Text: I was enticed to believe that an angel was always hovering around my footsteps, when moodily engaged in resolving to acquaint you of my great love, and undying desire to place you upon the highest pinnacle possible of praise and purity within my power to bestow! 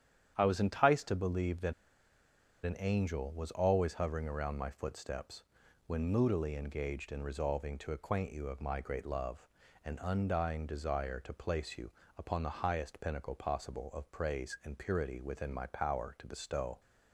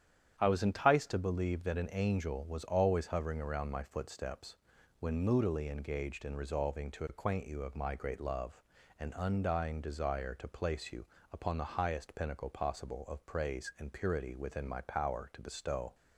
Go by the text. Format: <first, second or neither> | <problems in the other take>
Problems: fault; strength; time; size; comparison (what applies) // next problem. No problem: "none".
second | starts louder than the rest; strong; until 1.3 s; 9.5 dB; strong in the second // pauses between "that" and "an"; noticeable; at 1.7 s; 0.92 s long // pauses between "you" and "upon"; slight; at 11.8 s; 0.28 s long; slight in the second